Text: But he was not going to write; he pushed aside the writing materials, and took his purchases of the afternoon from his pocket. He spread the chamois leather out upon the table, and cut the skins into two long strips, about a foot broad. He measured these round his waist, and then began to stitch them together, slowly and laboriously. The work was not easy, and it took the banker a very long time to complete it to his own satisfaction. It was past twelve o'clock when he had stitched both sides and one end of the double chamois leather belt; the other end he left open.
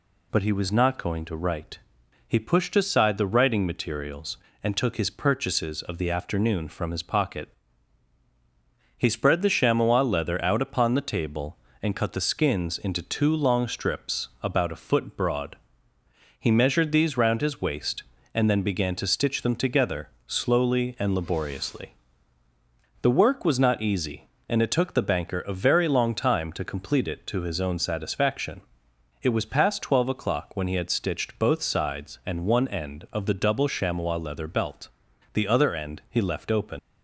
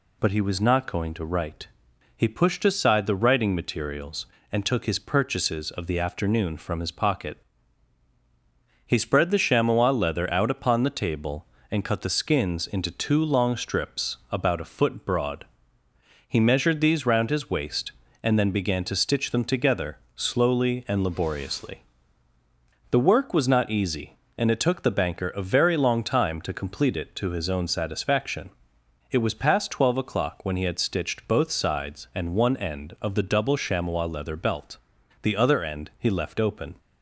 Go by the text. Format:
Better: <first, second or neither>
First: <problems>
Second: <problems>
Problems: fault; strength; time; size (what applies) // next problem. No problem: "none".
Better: second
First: leaves "open" unfinished; at 36.7 s; 105 ms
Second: none